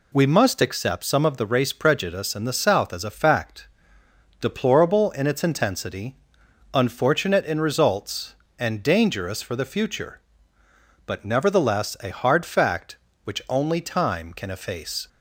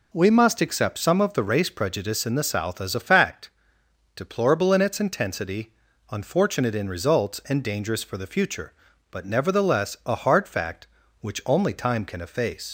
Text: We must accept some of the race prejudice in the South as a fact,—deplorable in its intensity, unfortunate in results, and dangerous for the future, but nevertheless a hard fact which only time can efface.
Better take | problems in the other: first | leaves "efface" unfinished; at 12.6 s; 75 ms

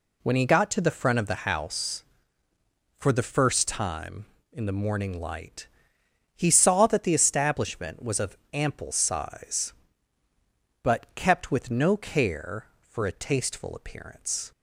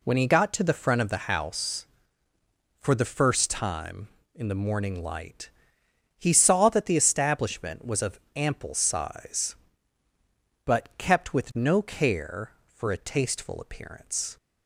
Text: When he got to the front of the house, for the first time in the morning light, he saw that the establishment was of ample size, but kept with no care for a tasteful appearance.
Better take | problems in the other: neither | pauses between "of" and "ample"; slight; the same in both

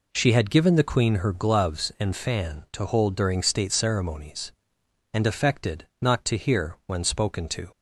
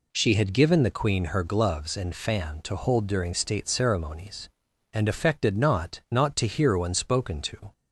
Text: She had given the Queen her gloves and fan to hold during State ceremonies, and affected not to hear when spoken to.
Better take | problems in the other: first | says "not" twice; at 6.1 s

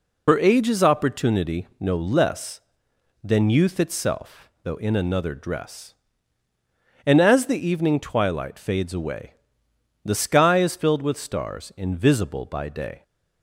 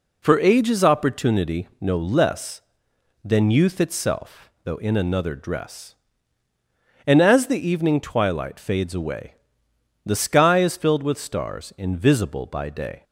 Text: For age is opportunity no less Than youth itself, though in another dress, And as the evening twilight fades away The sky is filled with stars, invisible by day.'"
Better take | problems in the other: second | loses the start of "For"; at 0.2 s; 50 ms // pauses between "away" and "The"; noticeable; at 9.3 s; 0.72 s long; noticeable in the second

